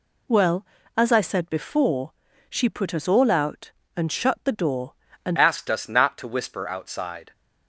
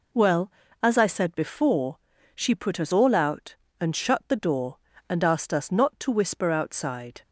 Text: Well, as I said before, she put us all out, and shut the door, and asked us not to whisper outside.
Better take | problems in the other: second | changes voice at "asked"; from 5.3 s on; 2.0 s long

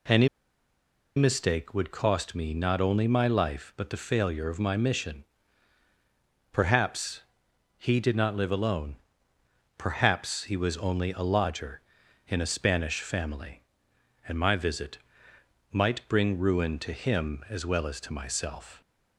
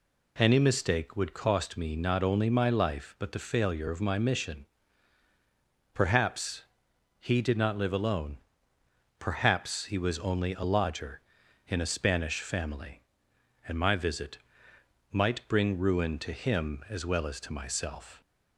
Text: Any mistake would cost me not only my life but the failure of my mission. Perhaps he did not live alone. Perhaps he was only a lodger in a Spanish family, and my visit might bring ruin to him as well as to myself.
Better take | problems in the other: second | pauses between "Any" and "mistake"; noticeable; at 0.2 s; 0.88 s long // pauses between "Perhaps" and "he"; noticeable; at 7.2 s; 0.54 s long; noticeable in the second // pauses between "visit" and "might"; noticeable; at 14.9 s; 0.74 s long; noticeable in the second

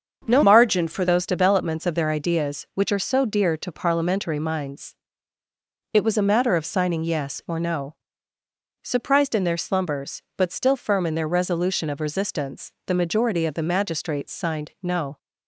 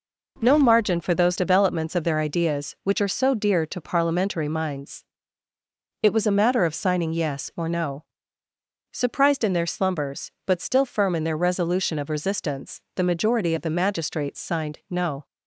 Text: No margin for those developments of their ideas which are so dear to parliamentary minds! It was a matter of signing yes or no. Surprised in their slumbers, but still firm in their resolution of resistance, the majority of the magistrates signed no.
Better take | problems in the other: second | starts louder than the rest; until 1.2 s; 6.5 dB // changes voice from "margin" to "for"; from 0.4 to 1.0 s; 0.6 s long

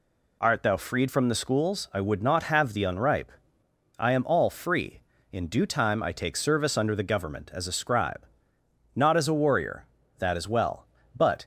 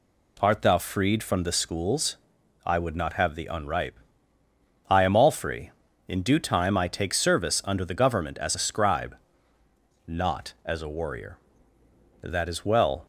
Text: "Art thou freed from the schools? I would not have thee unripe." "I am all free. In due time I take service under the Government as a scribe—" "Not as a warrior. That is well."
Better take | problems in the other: second | goes on to say "But"; slight; from 11.1 s on; 0.30 s long

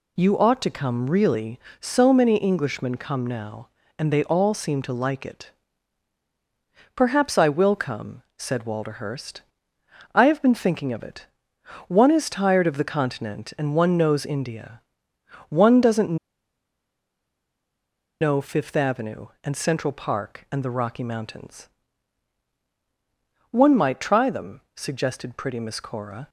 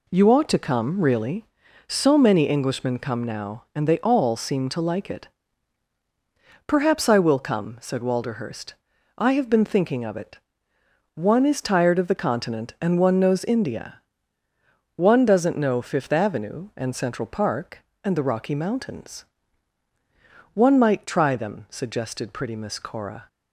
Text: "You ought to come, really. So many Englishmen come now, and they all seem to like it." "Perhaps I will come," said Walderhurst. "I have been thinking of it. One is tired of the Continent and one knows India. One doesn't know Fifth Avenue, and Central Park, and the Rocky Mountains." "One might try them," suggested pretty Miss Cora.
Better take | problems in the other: second | pauses between "doesn't" and "know"; strong; at 16.1 s; 2.0 s long

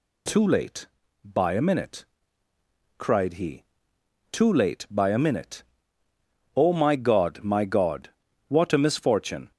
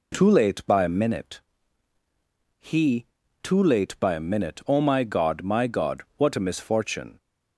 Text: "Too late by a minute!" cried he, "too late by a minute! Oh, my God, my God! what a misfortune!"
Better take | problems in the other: first | skips "cried"; at 2.0 s

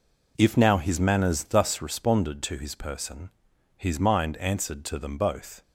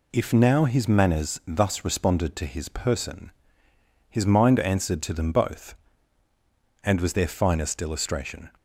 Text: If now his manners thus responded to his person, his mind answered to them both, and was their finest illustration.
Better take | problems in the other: second | stops before "and was their finest illustration"; at 5.6 s

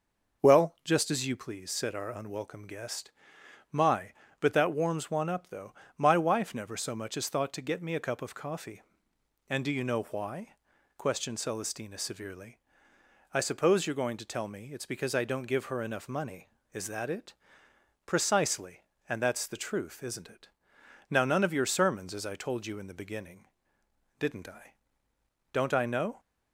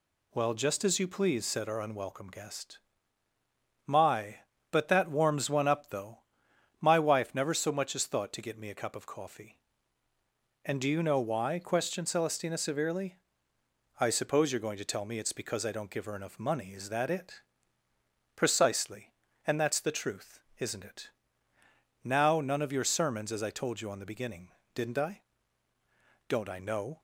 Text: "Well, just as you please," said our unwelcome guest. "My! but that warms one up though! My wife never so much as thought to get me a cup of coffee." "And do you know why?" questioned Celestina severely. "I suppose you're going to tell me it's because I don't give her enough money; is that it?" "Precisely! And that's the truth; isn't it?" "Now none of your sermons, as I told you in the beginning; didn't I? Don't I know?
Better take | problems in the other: first | says "on" for "in"; at 23.9 s

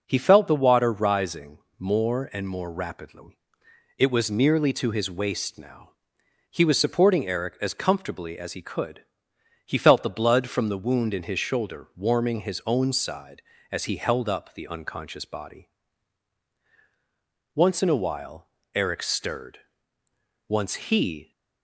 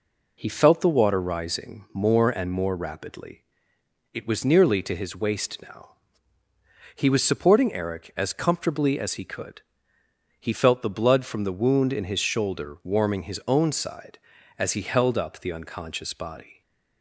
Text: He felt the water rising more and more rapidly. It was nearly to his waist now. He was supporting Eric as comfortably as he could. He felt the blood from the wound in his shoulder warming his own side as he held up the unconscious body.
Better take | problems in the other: second | pauses between "rising" and "more"; slight; at 1.5 s; 0.20 s long // goes on to say "Once in a while Eric stirred Once he"; strong; from 17.5 s on; 3.7 s long

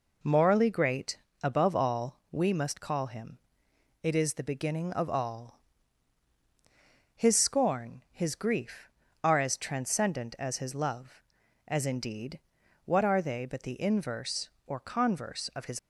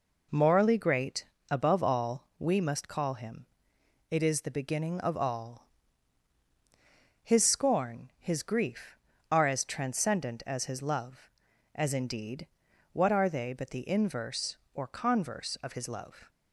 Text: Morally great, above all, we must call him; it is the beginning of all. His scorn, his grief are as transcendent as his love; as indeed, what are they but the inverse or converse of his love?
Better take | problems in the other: second | stops before "love"; at 15.7 s

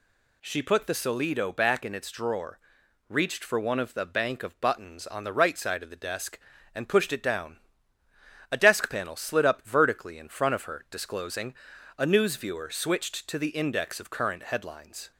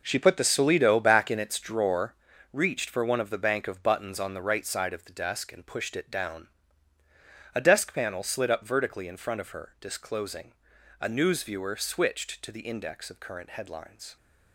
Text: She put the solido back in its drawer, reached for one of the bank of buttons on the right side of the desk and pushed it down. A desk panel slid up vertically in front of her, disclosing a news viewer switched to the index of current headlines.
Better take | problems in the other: first | gets quieter; strong; throughout; 10.5 dB // pauses between "disclosing" and "a"; noticeable; at 10.5 s; 0.48 s long; noticeable in the first

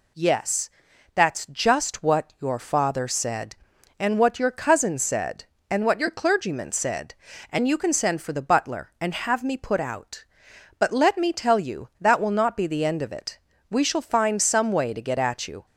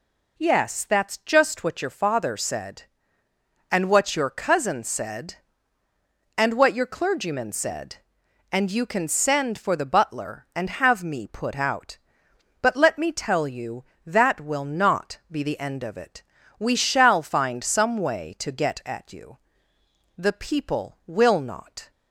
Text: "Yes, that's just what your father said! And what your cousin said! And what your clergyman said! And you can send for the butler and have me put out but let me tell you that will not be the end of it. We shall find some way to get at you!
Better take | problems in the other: first | goes on to say "The people will not"; strong; from 20.1 s on; 1.7 s long

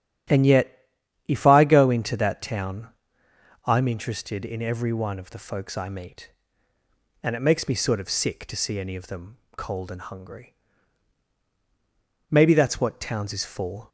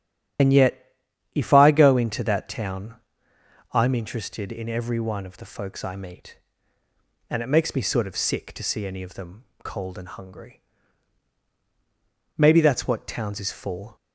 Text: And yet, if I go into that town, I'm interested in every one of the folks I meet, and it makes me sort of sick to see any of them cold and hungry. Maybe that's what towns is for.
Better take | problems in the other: first | loses the start of "And"; at 0.3 s; 55 ms // starts louder than the rest; strong; until 1.8 s; 10.5 dB; strong in the first // pauses between "them" and "cold"; slight; at 9.4 s; 0.20 s long; slight in the first

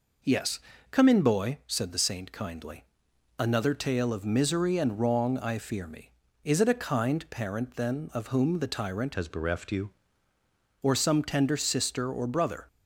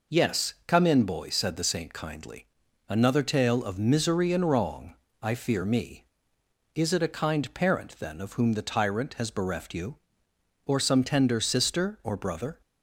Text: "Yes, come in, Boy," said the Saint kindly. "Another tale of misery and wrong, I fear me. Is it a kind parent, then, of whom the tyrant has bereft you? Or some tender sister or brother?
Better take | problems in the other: second | changes voice from "has" to "you"; from 9.1 to 9.9 s; 0.8 s long

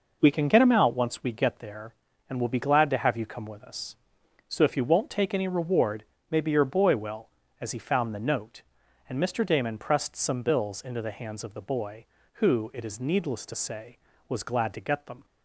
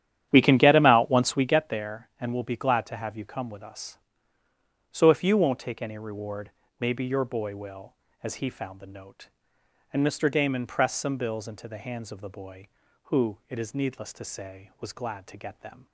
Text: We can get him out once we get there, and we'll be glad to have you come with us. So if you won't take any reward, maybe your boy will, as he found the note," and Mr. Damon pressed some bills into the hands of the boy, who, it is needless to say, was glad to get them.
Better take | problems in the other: first | starts louder than the rest; strong; until 1.5 s; 11 dB

